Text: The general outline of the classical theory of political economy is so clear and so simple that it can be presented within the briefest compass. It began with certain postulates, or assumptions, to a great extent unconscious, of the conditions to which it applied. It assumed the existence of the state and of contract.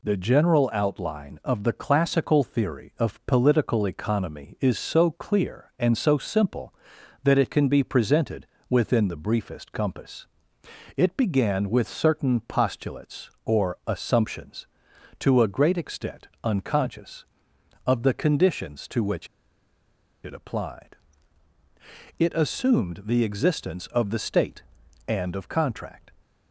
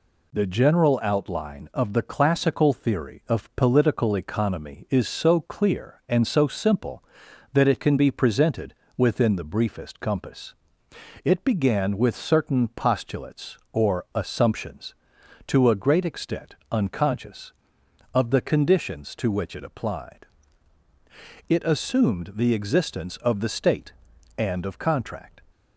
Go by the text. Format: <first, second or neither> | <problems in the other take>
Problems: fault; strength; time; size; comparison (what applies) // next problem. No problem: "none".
second | pauses between "presented" and "within"; slight; at 8.4 s; 0.22 s long; slight in the second // pauses between "extent" and "unconscious"; slight; at 16.2 s; 0.16 s long; slight in the second // pauses between "which" and "it"; noticeable; at 19.2 s; 0.97 s long